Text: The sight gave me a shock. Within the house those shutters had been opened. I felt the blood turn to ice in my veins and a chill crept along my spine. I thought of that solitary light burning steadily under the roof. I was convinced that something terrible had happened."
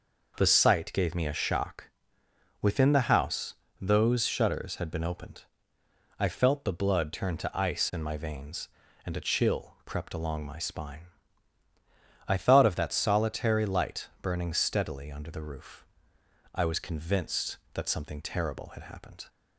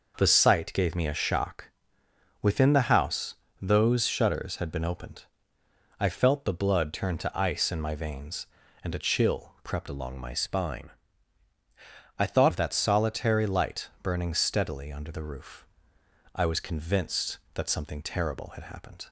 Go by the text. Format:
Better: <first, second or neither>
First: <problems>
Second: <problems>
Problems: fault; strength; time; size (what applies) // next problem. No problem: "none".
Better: first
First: pauses between "house" and "those"; slight; at 3.5 s; 0.28 s long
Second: pauses between "house" and "those"; slight; at 3.3 s; 0.28 s long // changes voice from "along" to "thought"; from 9.8 to 12.5 s; 2.7 s long